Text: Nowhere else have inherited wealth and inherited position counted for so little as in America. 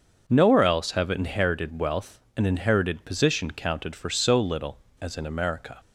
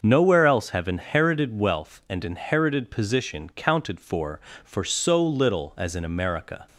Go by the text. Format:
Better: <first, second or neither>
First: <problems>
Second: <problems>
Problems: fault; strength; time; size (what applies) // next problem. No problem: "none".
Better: first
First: starts louder than the rest; until 1.2 s; 6.5 dB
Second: starts louder than the rest; until 1.0 s; 6.5 dB // says "for" twice; at 4.6 s